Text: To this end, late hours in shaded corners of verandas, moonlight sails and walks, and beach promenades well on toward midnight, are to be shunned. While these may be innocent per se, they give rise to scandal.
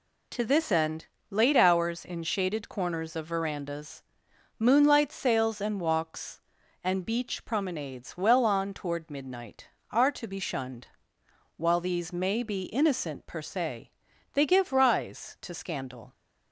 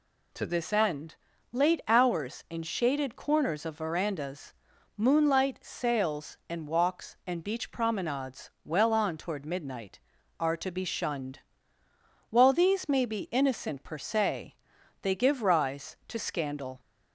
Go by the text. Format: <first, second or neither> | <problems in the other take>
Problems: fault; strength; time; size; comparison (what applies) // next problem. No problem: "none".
neither | none